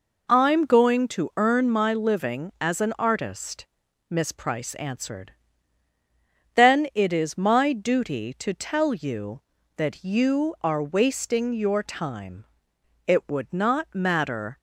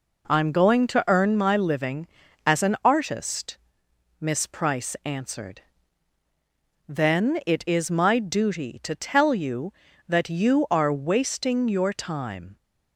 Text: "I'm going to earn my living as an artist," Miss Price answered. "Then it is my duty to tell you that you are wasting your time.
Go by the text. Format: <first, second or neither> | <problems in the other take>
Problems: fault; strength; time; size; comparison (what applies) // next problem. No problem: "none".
second | goes on to say "It would not matter"; from 13.0 s on; 1.5 s long